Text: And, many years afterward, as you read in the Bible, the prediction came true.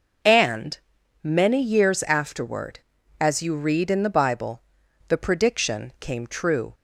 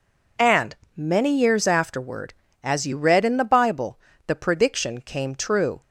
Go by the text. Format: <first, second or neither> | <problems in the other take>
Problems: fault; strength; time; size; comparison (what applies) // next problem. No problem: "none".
neither | none